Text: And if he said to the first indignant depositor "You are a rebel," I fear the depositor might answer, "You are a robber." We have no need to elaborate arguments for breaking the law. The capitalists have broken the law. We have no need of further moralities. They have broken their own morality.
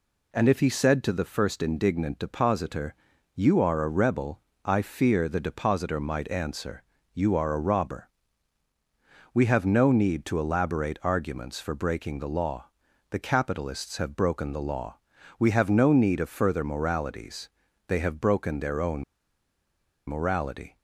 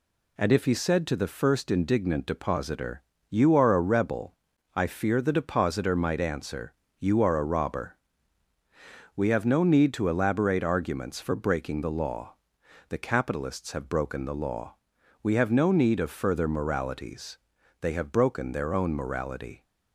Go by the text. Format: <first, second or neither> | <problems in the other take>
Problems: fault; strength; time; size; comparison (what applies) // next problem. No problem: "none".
second | pauses between "depositor" and "You"; at 2.9 s; 0.40 s long; slight in the second // pauses between "own" and "morality"; at 19.0 s; 1.0 s long